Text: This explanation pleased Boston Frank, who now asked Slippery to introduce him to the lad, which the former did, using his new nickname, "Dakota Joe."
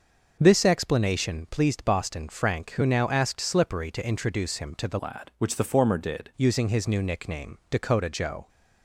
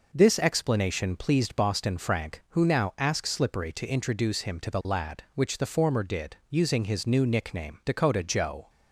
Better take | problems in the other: second | starts louder than the rest; noticeable; until 1.4 s; 6 dB // changes voice from "lad" to "did"; from 5.0 to 6.3 s; 1.3 s long

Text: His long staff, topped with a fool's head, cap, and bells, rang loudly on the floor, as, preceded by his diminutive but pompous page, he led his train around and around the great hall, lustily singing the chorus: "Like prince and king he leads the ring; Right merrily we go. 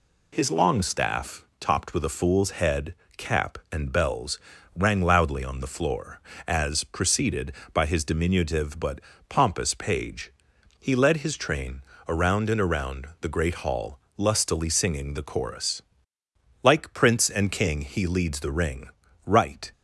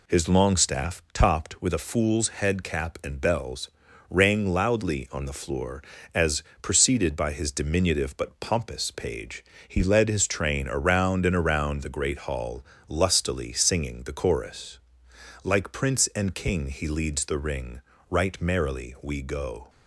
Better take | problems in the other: second | pauses between "but" and "pompous"; slight; at 8.9 s; 0.30 s long // pauses between "train" and "around"; slight; at 11.8 s; 0.26 s long // stops before "merrily we go"; at 19.7 s

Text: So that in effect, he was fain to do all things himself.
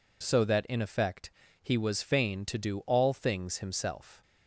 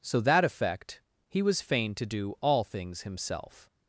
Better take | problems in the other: first | skips "in"; at 0.4 s

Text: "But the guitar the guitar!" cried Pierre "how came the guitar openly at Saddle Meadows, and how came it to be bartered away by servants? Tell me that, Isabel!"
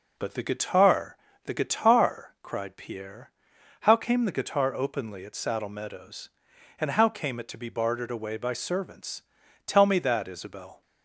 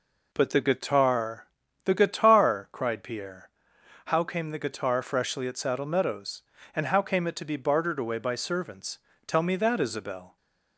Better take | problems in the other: first | pauses between "guitar" and "the"; slight; at 1.4 s; 0.36 s long; slight in the first // pauses between "Pierre" and "how"; noticeable; at 3.4 s; 0.56 s long; noticeable in the first // says "freshly" for "openly"; at 5.0 s

